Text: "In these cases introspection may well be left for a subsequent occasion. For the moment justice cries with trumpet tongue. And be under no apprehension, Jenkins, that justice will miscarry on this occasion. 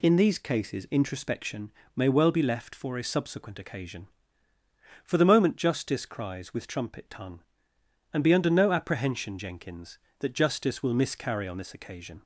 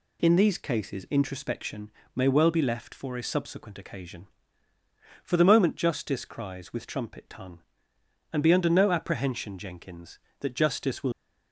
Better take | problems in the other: first | pauses between "introspection" and "may"; slight; at 1.9 s; 0.24 s long; slight in the first // stops before "miscarry on this occasion"; at 11.1 s

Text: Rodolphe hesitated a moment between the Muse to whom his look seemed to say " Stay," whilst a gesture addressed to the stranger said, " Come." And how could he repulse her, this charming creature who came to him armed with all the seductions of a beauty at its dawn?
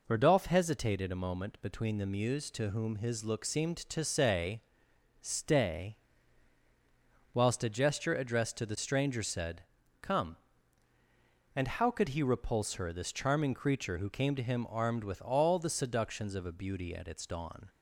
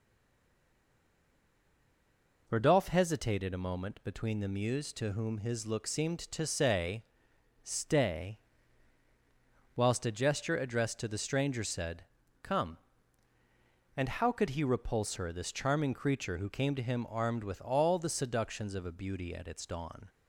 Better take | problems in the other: first | stays silent before the first word; until 2.4 s; 2.4 s long

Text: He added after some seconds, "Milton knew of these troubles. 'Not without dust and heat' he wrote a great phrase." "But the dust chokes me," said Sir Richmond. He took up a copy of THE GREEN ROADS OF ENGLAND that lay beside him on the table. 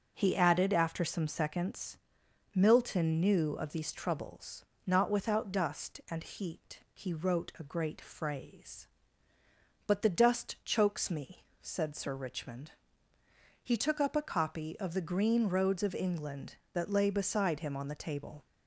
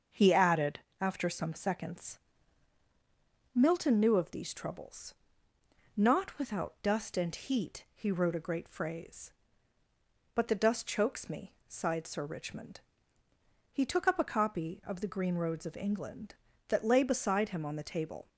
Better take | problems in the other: first | starts louder than the rest; until 1.3 s; 6.5 dB // pauses between "added" and "after"; slight; at 0.8 s; 0.20 s long // says "sighed" for "said"; at 11.6 s

